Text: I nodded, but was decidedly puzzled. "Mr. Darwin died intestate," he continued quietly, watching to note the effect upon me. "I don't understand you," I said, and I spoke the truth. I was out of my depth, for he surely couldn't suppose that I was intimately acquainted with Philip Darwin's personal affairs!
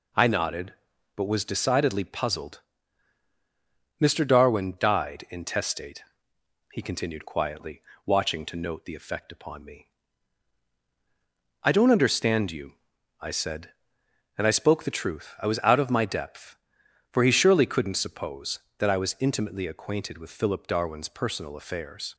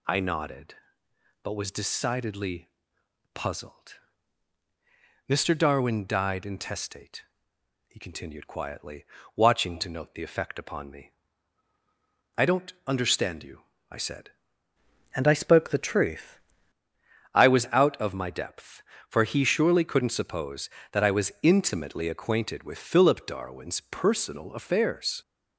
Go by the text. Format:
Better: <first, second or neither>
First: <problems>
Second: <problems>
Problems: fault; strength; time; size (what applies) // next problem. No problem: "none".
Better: first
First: none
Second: pauses between "decidedly" and "puzzled"; noticeable; at 2.6 s; 0.66 s long // changes voice from "and" to "truth"; from 15.1 to 16.3 s; 1.2 s long